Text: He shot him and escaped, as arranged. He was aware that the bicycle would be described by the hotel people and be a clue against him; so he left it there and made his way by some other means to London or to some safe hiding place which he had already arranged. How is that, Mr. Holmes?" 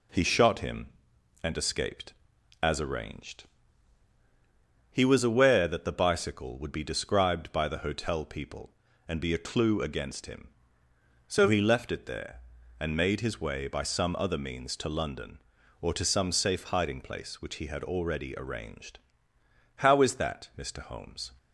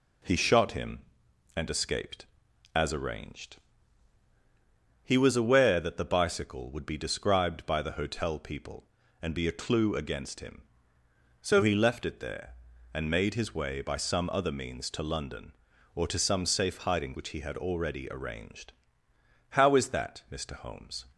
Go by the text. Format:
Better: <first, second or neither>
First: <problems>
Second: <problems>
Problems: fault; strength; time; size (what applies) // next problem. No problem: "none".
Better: first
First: none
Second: skips "place"; at 17.1 s